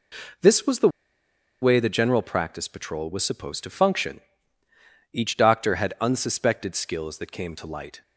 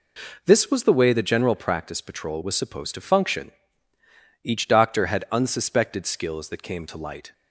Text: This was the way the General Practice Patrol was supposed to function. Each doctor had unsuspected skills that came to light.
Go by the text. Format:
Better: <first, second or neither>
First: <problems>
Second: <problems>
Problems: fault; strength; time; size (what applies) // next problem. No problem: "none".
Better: second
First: pauses between "the" and "way"; noticeable; at 0.8 s; 0.72 s long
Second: none